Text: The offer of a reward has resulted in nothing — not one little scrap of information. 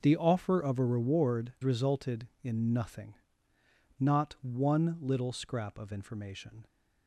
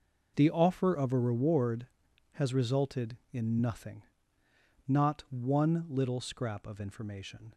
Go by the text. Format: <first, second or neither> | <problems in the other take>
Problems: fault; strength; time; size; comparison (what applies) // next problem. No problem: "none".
second | skips "has"; at 1.5 s